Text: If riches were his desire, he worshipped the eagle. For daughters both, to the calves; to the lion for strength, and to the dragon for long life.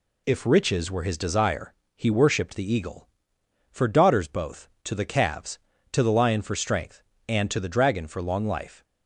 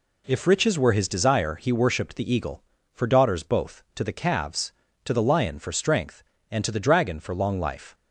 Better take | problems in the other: neither | none

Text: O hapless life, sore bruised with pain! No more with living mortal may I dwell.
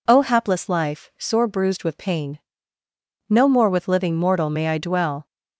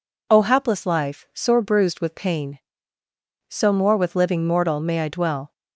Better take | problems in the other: first | says "So" for "No"; at 3.4 s

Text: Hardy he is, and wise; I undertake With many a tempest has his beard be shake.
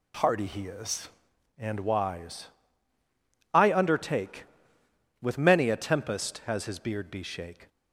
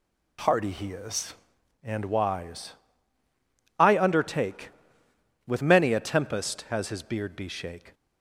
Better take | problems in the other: neither | none

